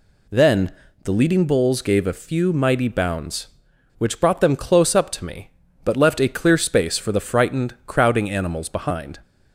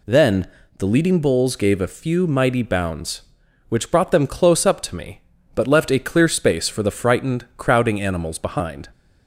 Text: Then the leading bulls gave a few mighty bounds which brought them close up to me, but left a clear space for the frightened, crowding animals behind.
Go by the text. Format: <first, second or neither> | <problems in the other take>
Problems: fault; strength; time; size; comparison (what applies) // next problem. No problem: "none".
neither | pauses between "Then" and "the"; slight; the same in both